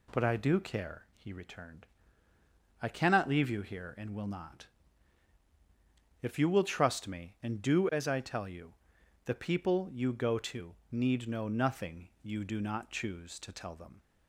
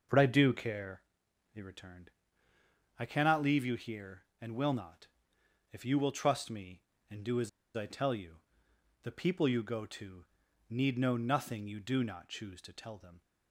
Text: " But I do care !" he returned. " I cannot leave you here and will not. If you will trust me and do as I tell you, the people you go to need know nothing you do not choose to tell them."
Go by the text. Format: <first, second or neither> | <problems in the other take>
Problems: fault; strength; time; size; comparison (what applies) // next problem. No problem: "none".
first | starts louder than the rest; until 1.3 s; 6.5 dB // pauses between "as" and "I"; slight; at 7.4 s; 0.26 s long // pauses between "to" and "need"; at 10.2 s; 0.44 s long; slight in the first